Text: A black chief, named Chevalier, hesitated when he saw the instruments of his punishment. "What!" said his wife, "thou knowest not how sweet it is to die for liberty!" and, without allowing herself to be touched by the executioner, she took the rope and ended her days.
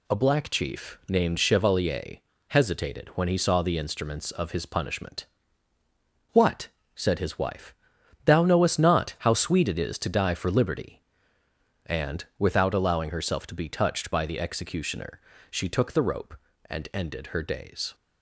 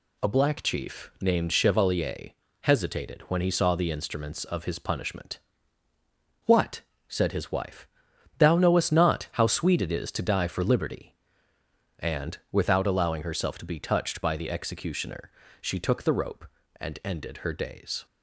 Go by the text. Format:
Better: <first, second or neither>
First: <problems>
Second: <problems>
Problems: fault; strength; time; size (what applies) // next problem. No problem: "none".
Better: neither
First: none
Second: none